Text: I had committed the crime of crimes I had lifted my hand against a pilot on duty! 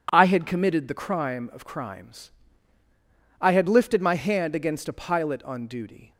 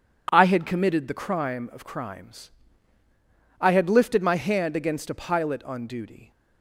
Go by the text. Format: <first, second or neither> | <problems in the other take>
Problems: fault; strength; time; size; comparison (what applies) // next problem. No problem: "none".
neither | pauses between "crimes" and "I"; the same in both